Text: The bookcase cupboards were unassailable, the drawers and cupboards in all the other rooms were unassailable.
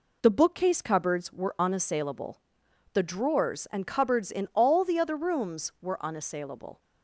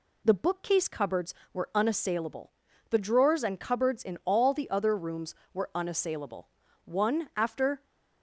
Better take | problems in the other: first | goes on to say "One after"; noticeable; from 6.8 s on; 0.98 s long

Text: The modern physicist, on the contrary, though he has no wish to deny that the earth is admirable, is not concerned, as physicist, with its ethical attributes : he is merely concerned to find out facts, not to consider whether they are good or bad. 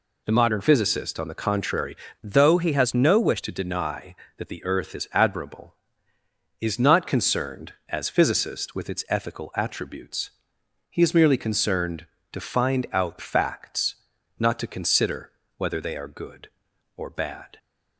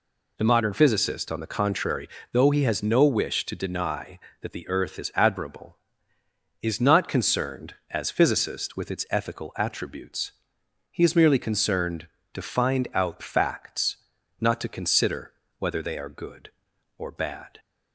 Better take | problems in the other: second | changes voice from "though" to "wish"; from 2.2 to 3.4 s; 1.2 s long // pauses between "consider" and "whether"; slight; at 15.3 s; 0.26 s long; slight in the second

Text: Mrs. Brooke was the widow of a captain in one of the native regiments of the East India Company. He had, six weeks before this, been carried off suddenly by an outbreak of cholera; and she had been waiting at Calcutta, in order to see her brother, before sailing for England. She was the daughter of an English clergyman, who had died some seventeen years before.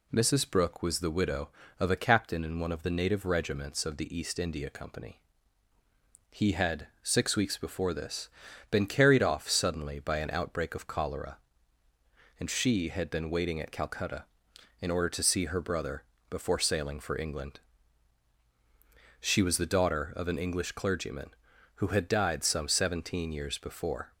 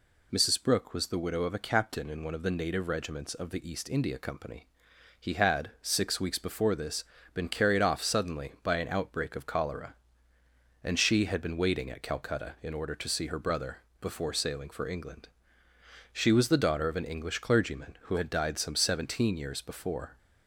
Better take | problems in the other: neither | none

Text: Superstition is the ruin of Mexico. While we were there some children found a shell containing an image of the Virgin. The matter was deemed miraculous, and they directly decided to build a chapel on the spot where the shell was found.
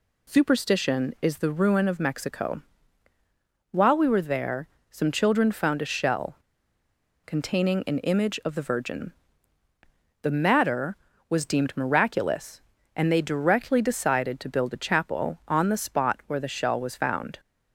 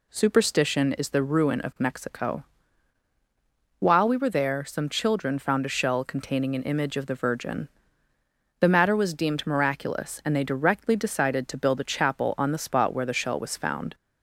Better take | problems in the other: second | pauses between "there" and "some"; slight; at 4.6 s; 0.22 s long // pauses between "shell" and "containing"; noticeable; at 6.3 s; 0.89 s long // pauses between "an" and "image"; slight; at 7.9 s; 0.16 s long

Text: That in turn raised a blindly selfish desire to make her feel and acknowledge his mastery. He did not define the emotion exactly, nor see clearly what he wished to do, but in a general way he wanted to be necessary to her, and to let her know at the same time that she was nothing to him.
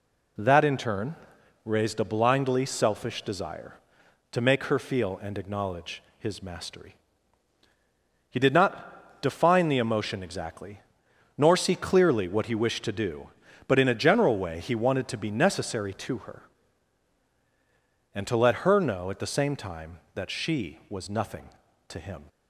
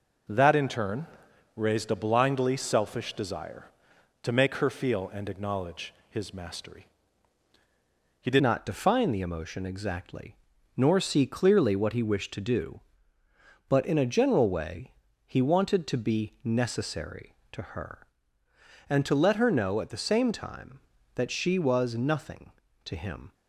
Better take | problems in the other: first | pauses between "turn" and "raised"; noticeable; at 1.0 s; 0.48 s long; noticeable in the first // pauses between "acknowledge" and "his"; slight; at 5.9 s; 0.16 s long; slight in the first // changes voice at "not"; from 8.3 s on; 15.0 s long // pauses between "way" and "he"; slight; at 14.9 s; 0.32 s long

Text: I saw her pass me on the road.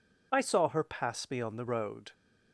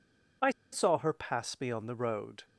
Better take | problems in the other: first | pauses between "I" and "saw"; slight; at 0.4 s; 0.22 s long

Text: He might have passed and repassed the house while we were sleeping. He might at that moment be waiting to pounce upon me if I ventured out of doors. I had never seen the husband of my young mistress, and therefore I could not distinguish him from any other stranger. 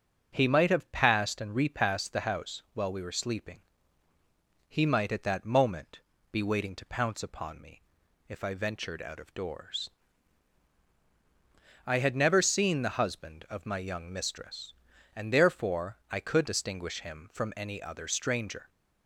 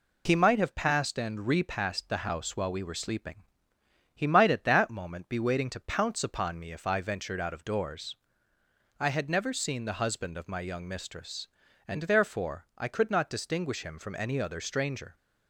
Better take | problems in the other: second | starts louder than the rest; until 1.3 s; 7 dB // pauses between "moment" and "be"; slight; at 5.9 s; 0.32 s long // pauses between "me" and "if"; at 7.8 s; 0.44 s long // skips "not"; at 16.4 s

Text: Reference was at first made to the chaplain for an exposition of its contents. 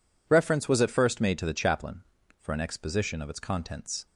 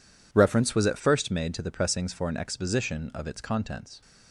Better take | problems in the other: first | says "pressings" for "chaplain"; at 1.7 s

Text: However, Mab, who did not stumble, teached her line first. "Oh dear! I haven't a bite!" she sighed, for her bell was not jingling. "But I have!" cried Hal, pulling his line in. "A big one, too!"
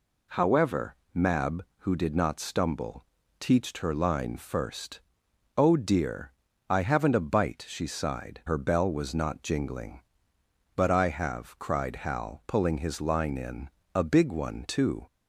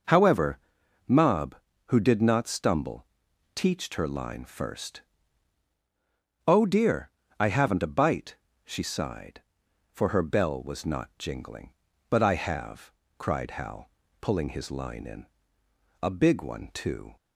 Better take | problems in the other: second | skips "for"; at 8.4 s

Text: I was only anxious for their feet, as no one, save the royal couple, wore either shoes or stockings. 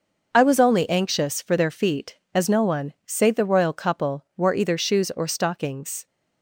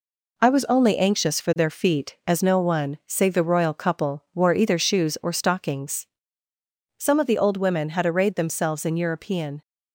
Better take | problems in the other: first | goes on to say "Some of the old women had arrayed themselves in European"; strong; from 6.9 s on; 2.6 s long

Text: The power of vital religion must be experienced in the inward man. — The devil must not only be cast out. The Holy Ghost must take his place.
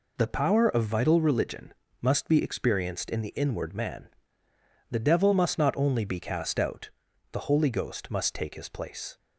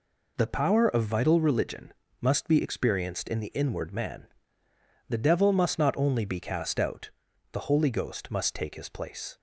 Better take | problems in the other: neither | pauses between "religion" and "must"; slight; the same in both

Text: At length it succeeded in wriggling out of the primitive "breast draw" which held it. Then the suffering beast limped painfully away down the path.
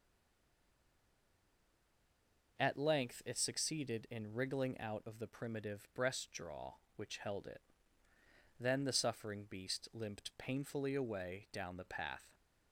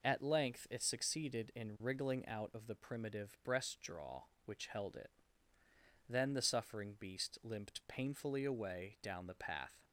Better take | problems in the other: second | stays silent before the first word; strong; until 2.5 s; 2.5 s long

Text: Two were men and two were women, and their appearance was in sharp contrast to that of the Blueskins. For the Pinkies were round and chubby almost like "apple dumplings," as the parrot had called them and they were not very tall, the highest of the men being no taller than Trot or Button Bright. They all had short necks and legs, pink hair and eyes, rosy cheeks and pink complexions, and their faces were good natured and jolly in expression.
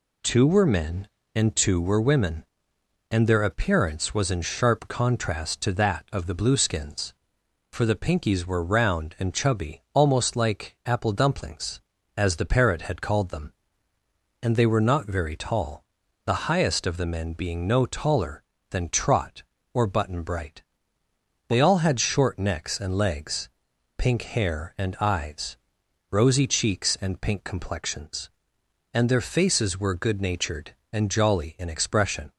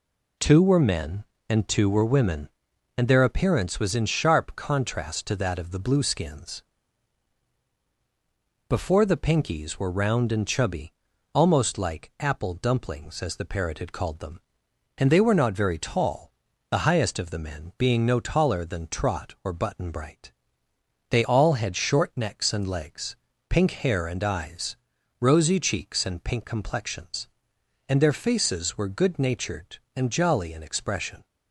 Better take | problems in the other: first | says "Before" for "For"; at 8.6 s // pauses between "chubby" and "almost"; at 10.9 s; 0.40 s long

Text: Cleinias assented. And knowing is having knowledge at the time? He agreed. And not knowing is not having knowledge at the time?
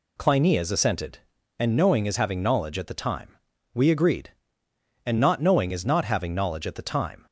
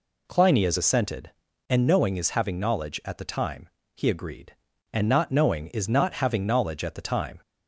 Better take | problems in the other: second | says "We" for "He"; at 3.7 s

